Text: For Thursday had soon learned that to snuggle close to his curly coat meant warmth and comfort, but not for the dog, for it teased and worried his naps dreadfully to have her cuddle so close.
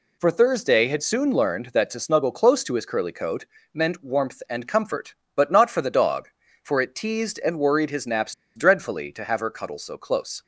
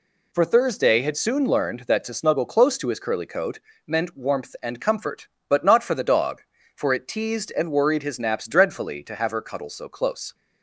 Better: second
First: pauses between "coat" and "meant"; slight; at 3.4 s; 0.26 s long // pauses between "naps" and "dreadfully"; slight; at 8.3 s; 0.22 s long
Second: pauses between "coat" and "meant"; slight; at 3.5 s; 0.25 s long

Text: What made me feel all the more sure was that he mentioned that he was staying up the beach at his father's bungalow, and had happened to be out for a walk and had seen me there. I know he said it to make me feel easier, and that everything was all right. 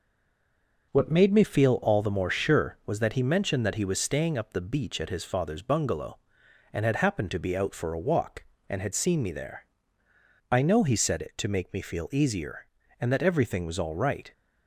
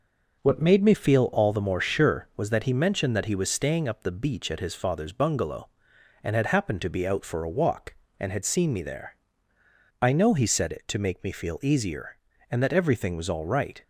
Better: second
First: stays silent before the first word; slight; until 0.9 s; 0.9 s long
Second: none

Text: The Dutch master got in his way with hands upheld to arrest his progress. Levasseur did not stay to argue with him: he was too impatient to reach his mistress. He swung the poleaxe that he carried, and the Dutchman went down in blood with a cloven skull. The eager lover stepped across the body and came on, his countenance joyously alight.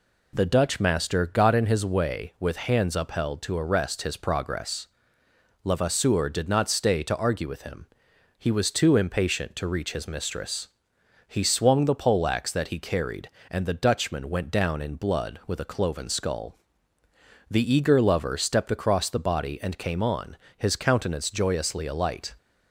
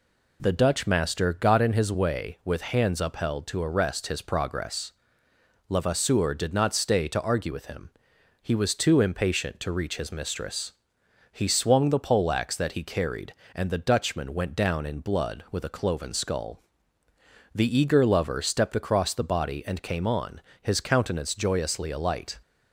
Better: neither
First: none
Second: none

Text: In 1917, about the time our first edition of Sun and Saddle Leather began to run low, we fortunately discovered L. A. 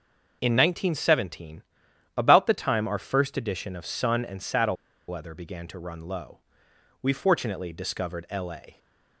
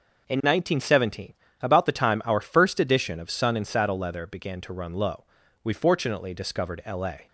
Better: second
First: pauses between "Saddle" and "Leather"; slight; at 4.7 s; 0.32 s long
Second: none

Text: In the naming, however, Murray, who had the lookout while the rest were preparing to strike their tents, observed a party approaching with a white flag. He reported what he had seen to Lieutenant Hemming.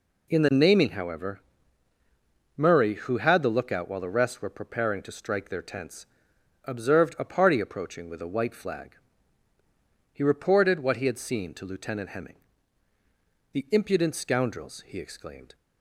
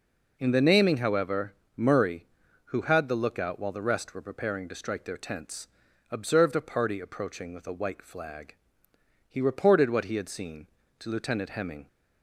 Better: second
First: goes on to say "The impudent scoundrels he exclaimed"; strong; from 13.5 s on; 2.0 s long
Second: none

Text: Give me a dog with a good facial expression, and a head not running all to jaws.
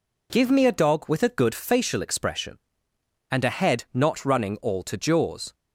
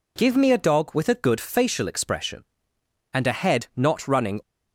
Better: first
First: none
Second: stops before "all to jaws"; at 4.4 s

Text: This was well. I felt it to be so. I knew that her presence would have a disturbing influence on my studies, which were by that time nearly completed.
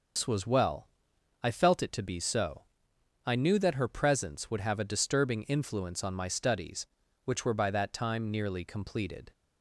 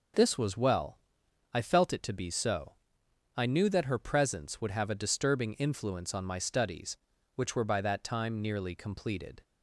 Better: second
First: loses the start of "This"; at 0.1 s; 125 ms // starts louder than the rest; noticeable; until 1.7 s; 6 dB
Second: none

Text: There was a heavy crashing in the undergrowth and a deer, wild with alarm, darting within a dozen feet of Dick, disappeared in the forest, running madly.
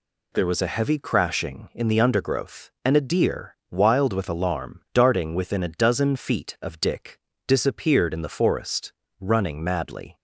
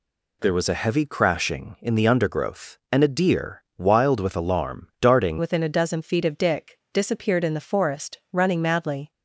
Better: first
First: none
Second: changes voice at "within"; from 5.3 s on; 3.8 s long

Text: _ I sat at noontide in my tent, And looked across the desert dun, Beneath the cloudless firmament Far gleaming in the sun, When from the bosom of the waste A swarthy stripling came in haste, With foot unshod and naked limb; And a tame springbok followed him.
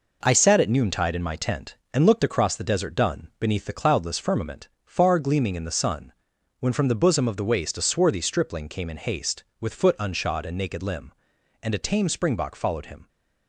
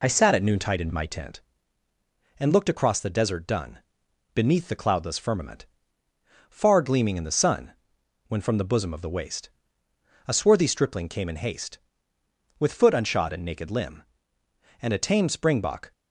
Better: first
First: pauses between "firmament" and "Far"; slight; at 4.6 s; 0.18 s long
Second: pauses between "firmament" and "Far"; noticeable; at 5.6 s; 0.82 s long // pauses between "waste" and "A"; noticeable; at 9.4 s; 0.78 s long // stops before "followed him"; at 15.9 s

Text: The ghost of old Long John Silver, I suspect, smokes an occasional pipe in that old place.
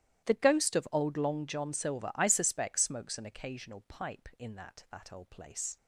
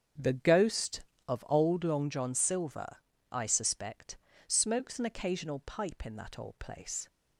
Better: second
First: starts louder than the rest; strong; until 1.3 s; 14 dB // says "that" twice; at 4.8 s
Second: starts louder than the rest; strong; until 1.4 s; 7.5 dB

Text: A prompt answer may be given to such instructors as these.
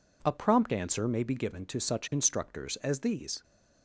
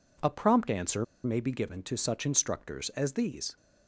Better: first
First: none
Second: pauses between "answer" and "may"; slight; at 1.0 s; 0.19 s long

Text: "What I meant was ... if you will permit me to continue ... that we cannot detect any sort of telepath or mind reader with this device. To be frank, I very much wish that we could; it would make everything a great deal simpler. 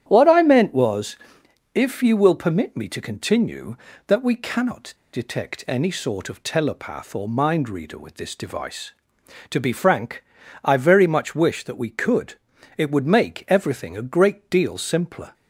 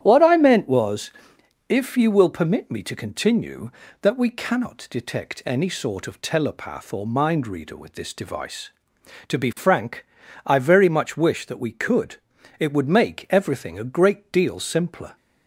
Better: second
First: starts louder than the rest; strong; until 1.0 s; 11 dB // pauses between "cannot" and "detect"; slight; at 4.9 s; 0.20 s long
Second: starts louder than the rest; strong; until 1.0 s; 11 dB

